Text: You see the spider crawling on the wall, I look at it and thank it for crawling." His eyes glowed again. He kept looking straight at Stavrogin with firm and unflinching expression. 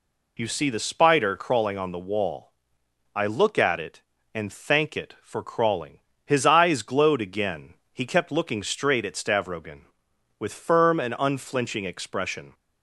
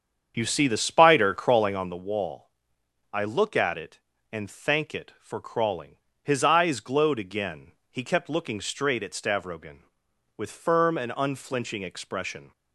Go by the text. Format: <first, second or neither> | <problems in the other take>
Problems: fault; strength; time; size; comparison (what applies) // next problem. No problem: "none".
first | starts louder than the rest; strong; until 2.0 s; 7.5 dB